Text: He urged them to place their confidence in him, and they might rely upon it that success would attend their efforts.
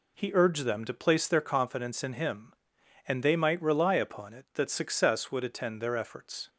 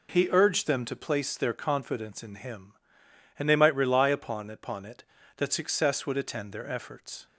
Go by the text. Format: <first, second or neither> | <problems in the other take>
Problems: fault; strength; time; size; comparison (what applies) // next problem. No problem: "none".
first | says "upon" twice; at 4.5 s